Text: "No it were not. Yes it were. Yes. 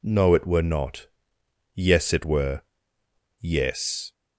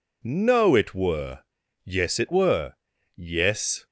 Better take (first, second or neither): first